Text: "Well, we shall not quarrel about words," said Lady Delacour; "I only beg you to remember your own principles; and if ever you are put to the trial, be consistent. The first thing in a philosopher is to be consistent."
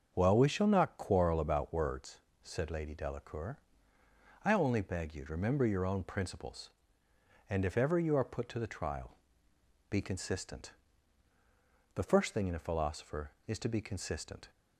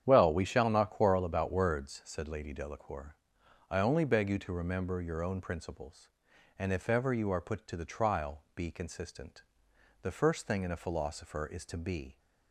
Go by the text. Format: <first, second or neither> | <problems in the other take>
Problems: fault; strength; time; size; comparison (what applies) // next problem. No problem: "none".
first | starts louder than the rest; strong; until 1.0 s; 9 dB; also in the first // stops before "consistent"; at 12.1 s